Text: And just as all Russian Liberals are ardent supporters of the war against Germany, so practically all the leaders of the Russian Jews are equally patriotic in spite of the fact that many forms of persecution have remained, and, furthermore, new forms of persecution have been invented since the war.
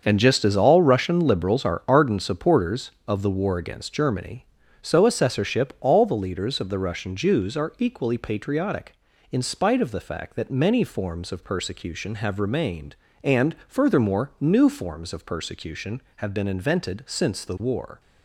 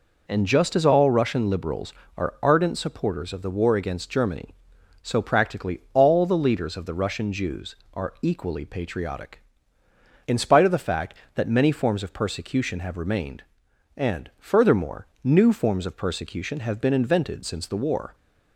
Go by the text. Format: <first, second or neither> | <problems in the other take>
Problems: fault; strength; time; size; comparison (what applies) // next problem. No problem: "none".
second | starts louder than the rest; until 1.0 s; 6.5 dB // says "assessorship" for "practically"; at 5.0 s